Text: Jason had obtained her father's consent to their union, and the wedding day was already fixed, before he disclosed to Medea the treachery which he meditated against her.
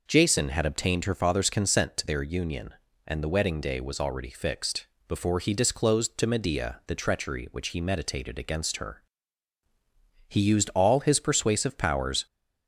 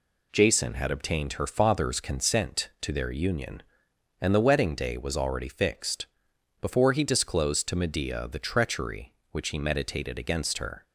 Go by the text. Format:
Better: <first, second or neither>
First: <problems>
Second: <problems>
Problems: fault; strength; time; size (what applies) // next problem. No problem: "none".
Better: second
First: goes on to say "He used all his persuasive powers"; strong; from 10.2 s on; 1.9 s long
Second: none